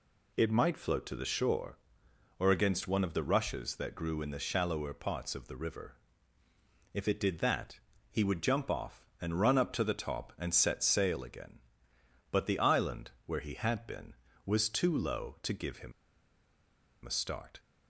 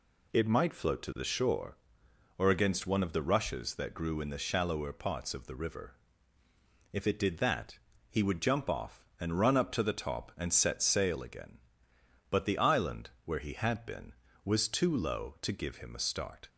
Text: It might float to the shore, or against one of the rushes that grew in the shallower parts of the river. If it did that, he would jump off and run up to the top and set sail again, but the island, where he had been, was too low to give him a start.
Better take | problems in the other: second | pauses between "him" and "a"; at 15.9 s; 1.1 s long

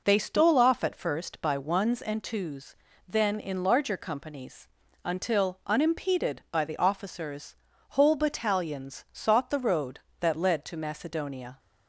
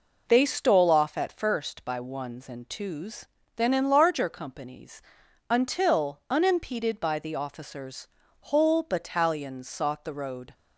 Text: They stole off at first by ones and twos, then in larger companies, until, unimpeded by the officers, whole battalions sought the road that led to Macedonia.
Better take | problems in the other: first | stops before "that led to Macedonia"; at 10.5 s

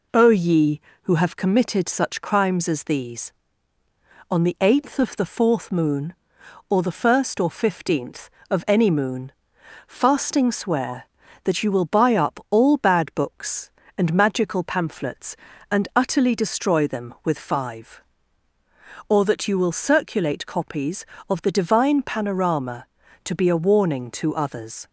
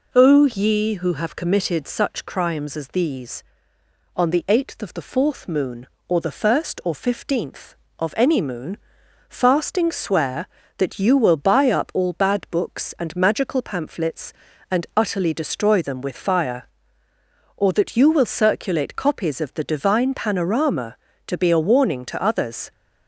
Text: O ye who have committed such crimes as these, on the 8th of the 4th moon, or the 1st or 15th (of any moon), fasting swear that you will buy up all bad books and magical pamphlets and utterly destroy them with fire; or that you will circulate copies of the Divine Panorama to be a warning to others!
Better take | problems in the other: second | says "five" for "fire"; at 17.3 s

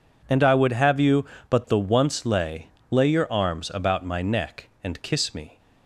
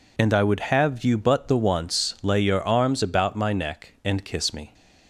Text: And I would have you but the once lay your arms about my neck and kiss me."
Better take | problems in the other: second | says "lay" twice; at 2.8 s

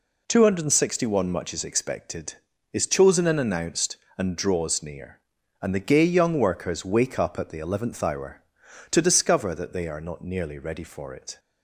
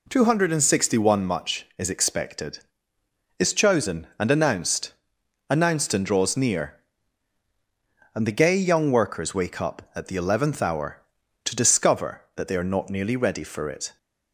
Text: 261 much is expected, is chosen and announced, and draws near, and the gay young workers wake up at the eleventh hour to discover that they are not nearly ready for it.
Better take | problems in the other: first | says "announced" twice; at 5.4 s

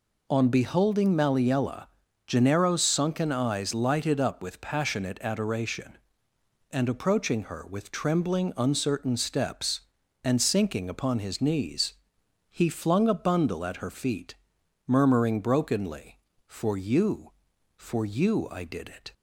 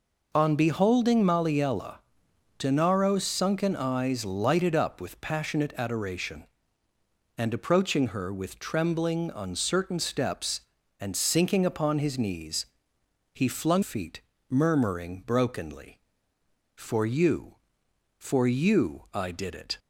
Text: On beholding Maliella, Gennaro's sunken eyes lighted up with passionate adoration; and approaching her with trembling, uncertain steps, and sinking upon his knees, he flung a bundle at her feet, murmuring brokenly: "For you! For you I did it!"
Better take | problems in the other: first | skips "a bundle at her"; at 13.8 s

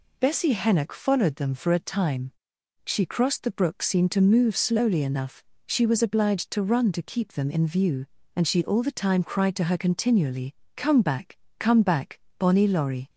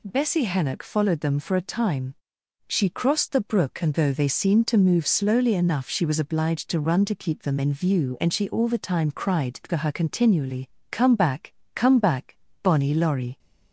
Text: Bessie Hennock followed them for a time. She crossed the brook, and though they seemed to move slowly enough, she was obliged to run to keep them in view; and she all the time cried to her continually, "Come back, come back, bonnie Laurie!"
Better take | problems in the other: second | skips "and though they"; at 3.8 s

